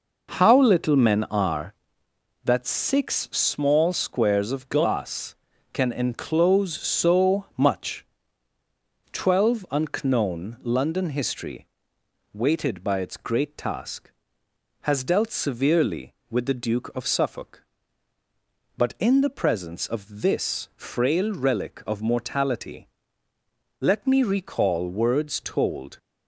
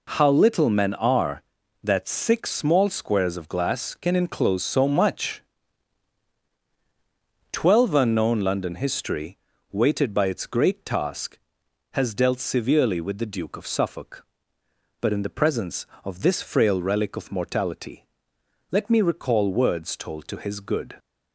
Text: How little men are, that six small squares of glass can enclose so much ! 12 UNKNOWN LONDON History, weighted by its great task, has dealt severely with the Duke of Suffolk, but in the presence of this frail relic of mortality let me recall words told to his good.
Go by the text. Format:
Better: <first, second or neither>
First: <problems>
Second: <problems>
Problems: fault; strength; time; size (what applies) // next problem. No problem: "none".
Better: second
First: pauses between "mortality" and "let"; noticeable; at 22.8 s; 0.92 s long // stops before "to his good"; at 25.9 s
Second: pauses between "mortality" and "let"; noticeable; at 18.0 s; 0.66 s long